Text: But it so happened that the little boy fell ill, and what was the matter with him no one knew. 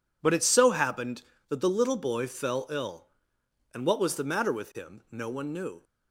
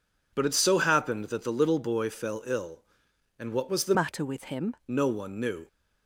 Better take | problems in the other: first | changes voice from "matter" to "him"; from 3.9 to 4.7 s; 0.8 s long

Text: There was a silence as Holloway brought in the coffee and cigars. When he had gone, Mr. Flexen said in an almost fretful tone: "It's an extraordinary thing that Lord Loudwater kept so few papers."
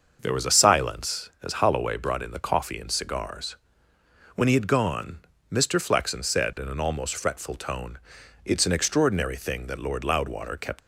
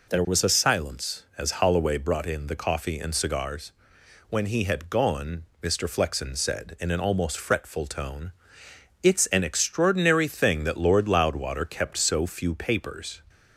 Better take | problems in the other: second | starts louder than the rest; until 1.2 s; 6 dB // stops before "so few papers"; at 10.8 s

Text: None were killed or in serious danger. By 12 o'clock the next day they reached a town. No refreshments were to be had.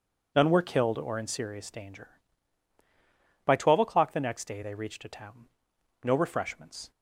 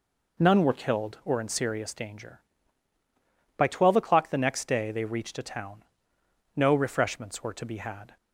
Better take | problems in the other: second | stops before "were to be had"; at 6.9 s

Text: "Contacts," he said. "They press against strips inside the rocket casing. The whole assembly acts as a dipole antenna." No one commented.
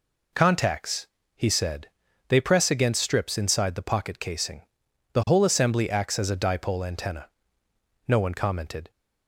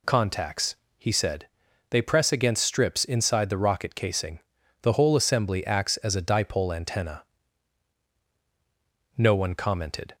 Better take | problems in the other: second | says "pocket" for "rocket"; at 3.8 s

